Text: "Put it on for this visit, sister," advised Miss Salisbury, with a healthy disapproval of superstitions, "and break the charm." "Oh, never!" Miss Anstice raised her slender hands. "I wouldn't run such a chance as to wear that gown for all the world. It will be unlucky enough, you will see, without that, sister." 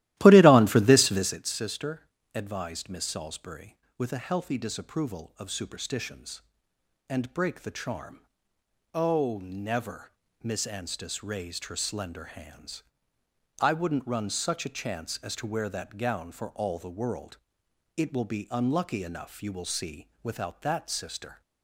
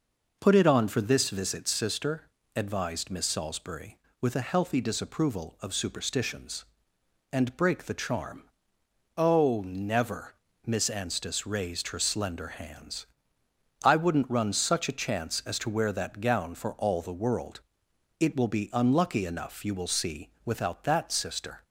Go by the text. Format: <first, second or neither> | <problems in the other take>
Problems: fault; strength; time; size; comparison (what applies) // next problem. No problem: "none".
second | starts louder than the rest; strong; until 1.4 s; 15.5 dB